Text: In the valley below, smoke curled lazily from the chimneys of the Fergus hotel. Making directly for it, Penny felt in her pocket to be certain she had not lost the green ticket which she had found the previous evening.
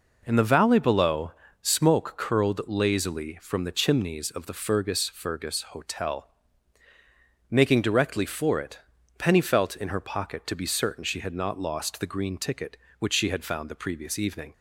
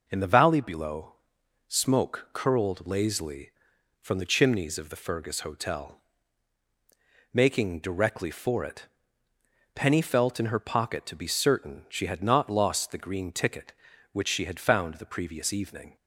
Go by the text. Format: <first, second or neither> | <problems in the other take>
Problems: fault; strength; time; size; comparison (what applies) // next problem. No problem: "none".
second | says "Fergus" twice; at 5.0 s